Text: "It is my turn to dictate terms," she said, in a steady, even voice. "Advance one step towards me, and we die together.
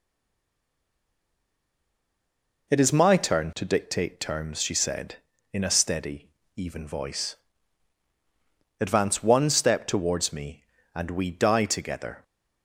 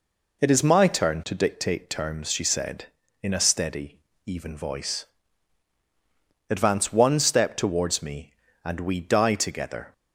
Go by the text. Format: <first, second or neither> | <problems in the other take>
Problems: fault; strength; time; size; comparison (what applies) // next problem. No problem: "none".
second | stays silent before the first word; strong; until 2.6 s; 2.6 s long